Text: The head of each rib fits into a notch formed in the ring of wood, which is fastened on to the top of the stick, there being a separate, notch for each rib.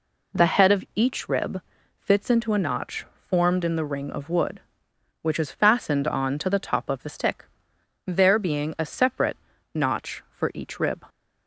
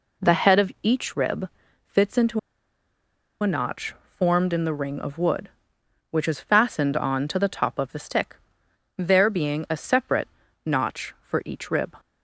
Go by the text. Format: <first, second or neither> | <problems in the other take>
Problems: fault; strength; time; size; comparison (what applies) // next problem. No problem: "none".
first | pauses between "rib" and "fits"; at 1.4 s; 0.40 s long; also in the first // pauses between "into" and "a"; at 2.3 s; 1.0 s long // pauses between "notch" and "formed"; slight; at 3.9 s; 0.16 s long; slight in the first